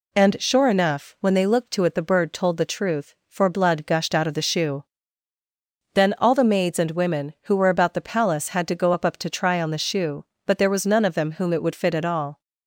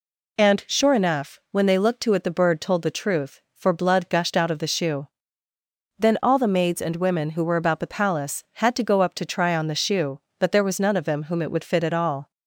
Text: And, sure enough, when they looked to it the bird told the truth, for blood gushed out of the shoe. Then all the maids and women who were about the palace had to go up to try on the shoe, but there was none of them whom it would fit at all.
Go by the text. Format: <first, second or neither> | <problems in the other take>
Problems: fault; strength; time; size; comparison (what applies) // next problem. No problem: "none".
second | says "up" twice; at 9.0 s